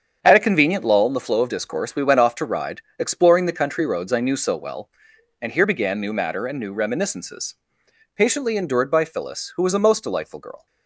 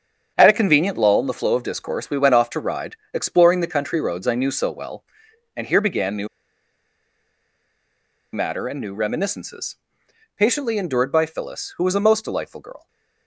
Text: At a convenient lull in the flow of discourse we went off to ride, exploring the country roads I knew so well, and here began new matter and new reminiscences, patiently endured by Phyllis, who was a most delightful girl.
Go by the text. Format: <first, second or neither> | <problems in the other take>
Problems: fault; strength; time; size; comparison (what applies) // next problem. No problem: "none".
first | starts louder than the rest; strong; until 1.3 s; 7.5 dB; strong in the first // pauses between "new" and "matter"; strong; at 6.2 s; 2.0 s long